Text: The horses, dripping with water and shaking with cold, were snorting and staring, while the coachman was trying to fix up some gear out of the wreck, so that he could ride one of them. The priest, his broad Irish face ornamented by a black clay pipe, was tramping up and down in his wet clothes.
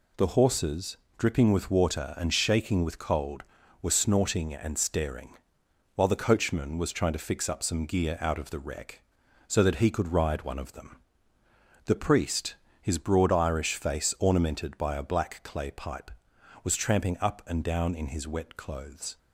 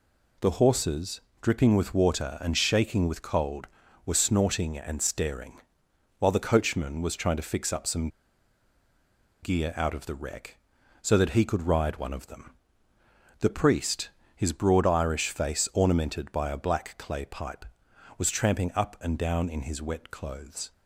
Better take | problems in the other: first | pauses between "some" and "gear"; strong; at 8.0 s; 1.3 s long

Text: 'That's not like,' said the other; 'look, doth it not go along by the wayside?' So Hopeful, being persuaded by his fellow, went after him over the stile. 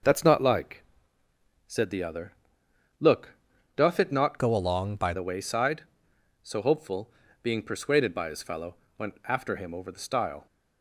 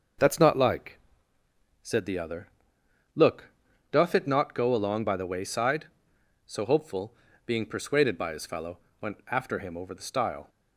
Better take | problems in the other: second | starts louder than the rest; until 1.8 s; 6 dB; noticeable in the second // changes voice from "go" to "by"; from 4.3 to 5.1 s; 0.8 s long

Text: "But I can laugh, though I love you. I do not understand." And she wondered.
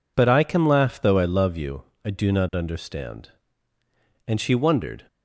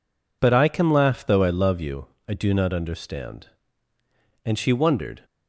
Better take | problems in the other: neither | none

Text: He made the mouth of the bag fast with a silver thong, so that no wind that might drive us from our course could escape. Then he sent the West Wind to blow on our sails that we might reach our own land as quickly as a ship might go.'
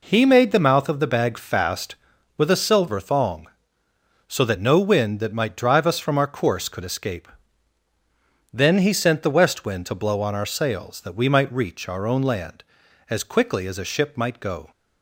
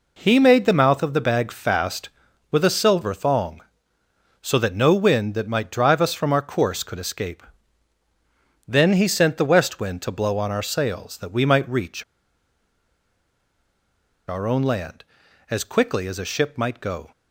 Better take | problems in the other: first | pauses between "reach" and "our"; strong; at 12.0 s; 2.2 s long

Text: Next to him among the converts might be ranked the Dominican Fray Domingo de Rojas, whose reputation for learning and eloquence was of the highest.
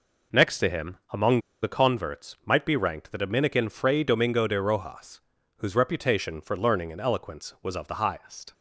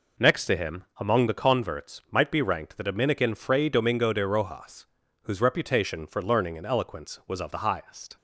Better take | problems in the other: second | pauses between "among" and "the"; slight; at 1.3 s; 0.23 s long

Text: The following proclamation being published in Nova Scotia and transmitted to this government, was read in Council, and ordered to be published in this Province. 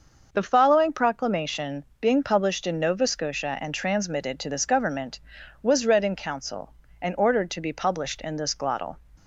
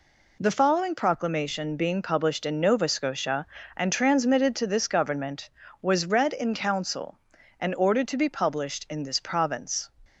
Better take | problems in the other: second | starts louder than the rest; noticeable; until 1.3 s; 6 dB // pauses between "proclamation" and "being"; slight; at 1.8 s; 0.16 s long // says "Glottal" for "Province"; at 8.5 s

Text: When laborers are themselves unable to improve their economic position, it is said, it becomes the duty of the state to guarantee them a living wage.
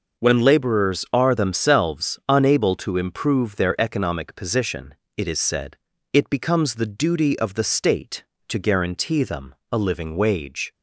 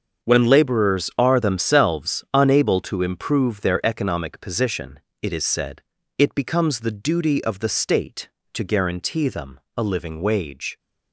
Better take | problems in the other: first | gets quieter; strong; throughout; 12.5 dB // pauses between "them" and "a"; slight; at 9.5 s; 0.18 s long; slight in the first

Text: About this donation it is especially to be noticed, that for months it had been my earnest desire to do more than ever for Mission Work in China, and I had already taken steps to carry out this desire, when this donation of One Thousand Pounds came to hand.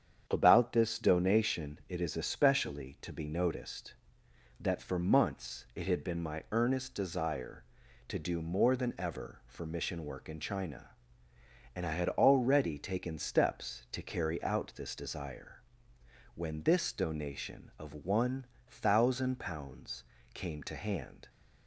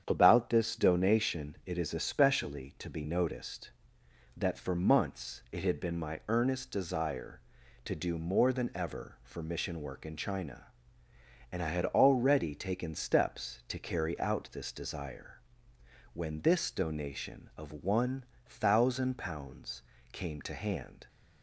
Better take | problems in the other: neither | starts louder than the rest; strong; the same in both // pauses between "One" and "Thousand"; slight; the same in both // pauses between "Pounds" and "came"; slight; the same in both

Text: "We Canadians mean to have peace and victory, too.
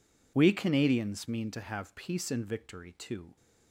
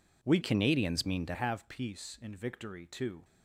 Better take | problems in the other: first | changes voice from "Canadians" to "to"; from 0.4 to 1.3 s; 0.9 s long

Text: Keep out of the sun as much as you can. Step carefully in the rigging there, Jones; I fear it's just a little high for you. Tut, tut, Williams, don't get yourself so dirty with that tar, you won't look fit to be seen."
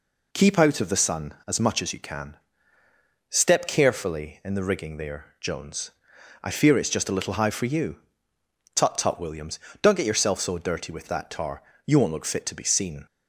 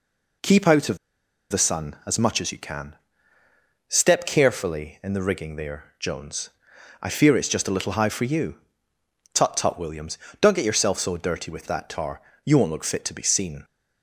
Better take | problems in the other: first | pauses between "of" and "the"; noticeable; at 0.9 s; 0.53 s long

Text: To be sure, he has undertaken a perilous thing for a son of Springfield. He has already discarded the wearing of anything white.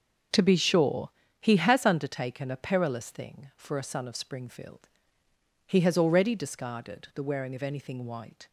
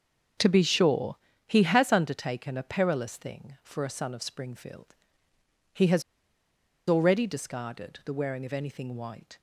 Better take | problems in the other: first | starts louder than the rest; until 1.7 s; 6.5 dB; also in the first // pauses between "has" and "already"; noticeable; at 6.0 s; 0.85 s long

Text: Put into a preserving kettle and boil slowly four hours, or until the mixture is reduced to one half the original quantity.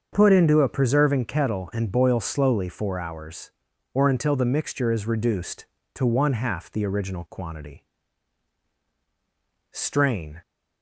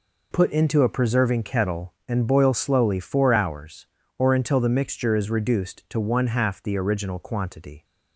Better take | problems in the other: second | starts louder than the rest; until 1.1 s; 6.5 dB // goes on to say "Strain"; noticeable; from 9.7 s on; 0.70 s long

